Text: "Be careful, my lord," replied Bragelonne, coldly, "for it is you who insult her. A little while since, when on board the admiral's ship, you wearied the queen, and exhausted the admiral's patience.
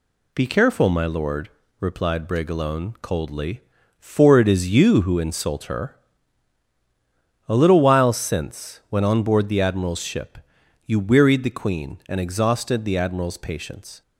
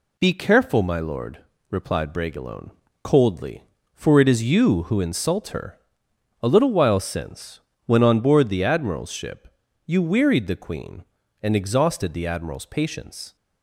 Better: neither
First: none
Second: none

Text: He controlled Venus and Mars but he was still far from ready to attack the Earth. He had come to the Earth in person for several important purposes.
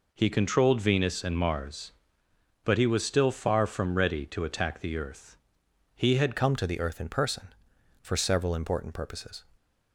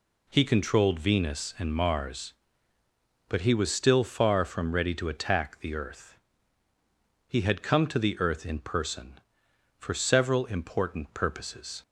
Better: second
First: changes voice at "come"; from 6.3 s on; 3.1 s long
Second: none

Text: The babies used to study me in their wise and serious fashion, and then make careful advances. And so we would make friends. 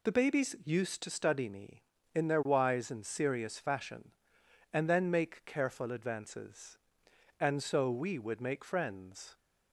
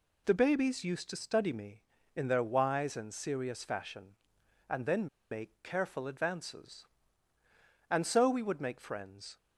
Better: first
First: none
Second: pauses between "then" and "make"; slight; at 5.0 s; 0.24 s long

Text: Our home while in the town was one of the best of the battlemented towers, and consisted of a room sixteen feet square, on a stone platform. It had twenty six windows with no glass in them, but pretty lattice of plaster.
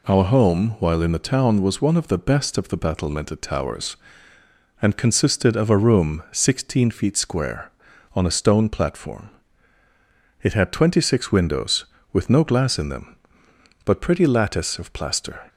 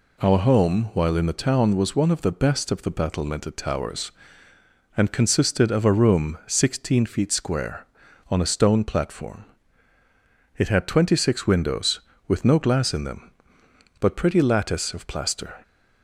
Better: neither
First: none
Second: none

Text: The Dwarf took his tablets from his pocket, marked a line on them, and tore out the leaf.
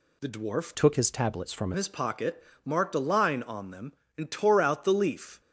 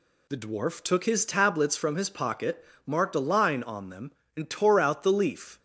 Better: second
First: changes voice from "took" to "from"; from 0.7 to 1.7 s; 1.0 s long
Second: none

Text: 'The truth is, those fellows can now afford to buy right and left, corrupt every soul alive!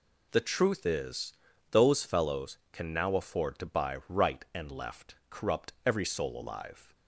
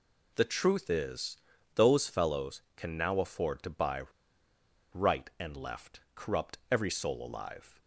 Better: first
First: none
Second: pauses between "buy" and "right"; noticeable; at 4.0 s; 0.90 s long

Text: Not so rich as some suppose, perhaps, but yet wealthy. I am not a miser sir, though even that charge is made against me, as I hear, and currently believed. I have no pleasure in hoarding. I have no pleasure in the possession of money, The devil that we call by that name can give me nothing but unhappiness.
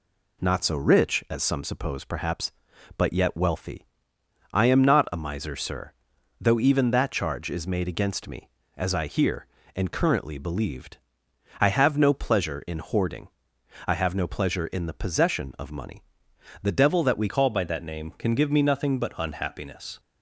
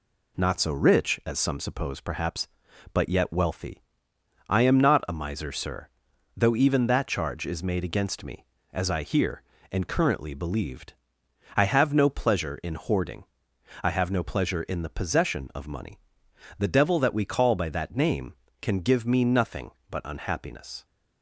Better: second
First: changes voice at "call"; from 17.2 s on; 2.7 s long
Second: none

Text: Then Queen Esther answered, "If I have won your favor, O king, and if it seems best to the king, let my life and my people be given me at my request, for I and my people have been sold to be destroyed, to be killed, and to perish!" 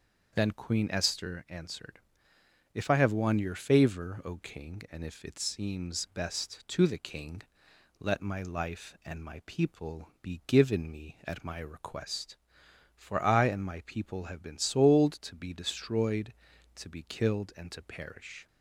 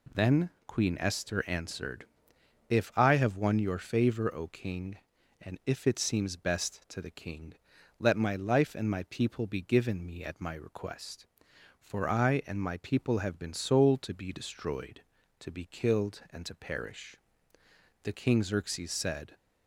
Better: first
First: none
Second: pauses between "Then" and "Queen"; slight; at 0.5 s; 0.16 s long // goes on to say "The King Xerxes said"; from 18.0 s on; 1.3 s long

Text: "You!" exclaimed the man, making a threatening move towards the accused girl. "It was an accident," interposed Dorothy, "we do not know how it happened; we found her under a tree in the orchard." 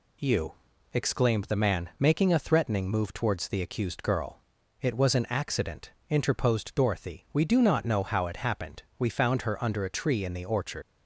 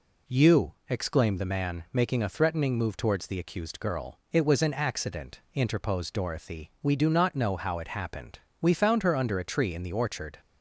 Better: second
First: leaves "orchard" unfinished; at 10.8 s; 100 ms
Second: none

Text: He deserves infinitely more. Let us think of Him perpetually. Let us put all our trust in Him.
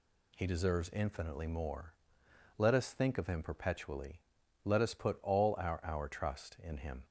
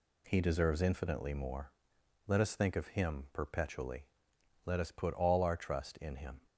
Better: second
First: says "our" twice; at 5.8 s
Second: none

